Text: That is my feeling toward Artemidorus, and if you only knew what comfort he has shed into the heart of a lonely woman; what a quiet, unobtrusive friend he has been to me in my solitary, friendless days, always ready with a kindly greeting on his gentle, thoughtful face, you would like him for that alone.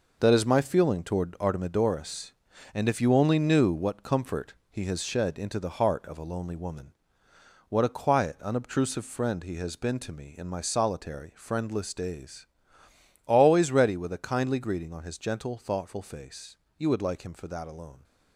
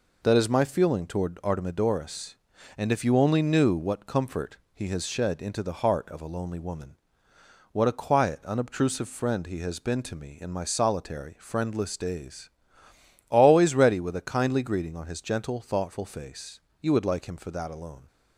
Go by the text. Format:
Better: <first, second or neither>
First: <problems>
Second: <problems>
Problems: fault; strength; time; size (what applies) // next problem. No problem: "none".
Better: second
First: gets quieter; strong; throughout; 8.5 dB // pauses between "comfort" and "he"; slight; at 4.5 s; 0.16 s long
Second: pauses between "comfort" and "he"; slight; at 4.5 s; 0.16 s long